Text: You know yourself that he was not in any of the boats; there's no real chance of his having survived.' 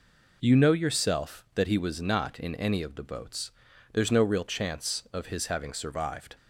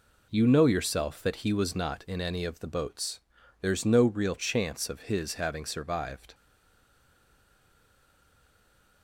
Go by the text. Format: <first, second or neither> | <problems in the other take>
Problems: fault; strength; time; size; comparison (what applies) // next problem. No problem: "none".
first | stays silent after the last word; strong; from 6.3 s on; 2.7 s long